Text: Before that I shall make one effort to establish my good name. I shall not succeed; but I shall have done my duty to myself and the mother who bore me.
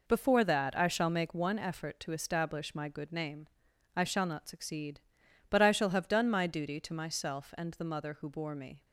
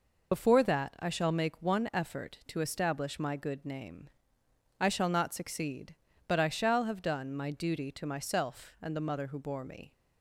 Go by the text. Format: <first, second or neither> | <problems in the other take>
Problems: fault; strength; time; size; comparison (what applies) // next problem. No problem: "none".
first | loses the start of "Before"; at 0.3 s; 85 ms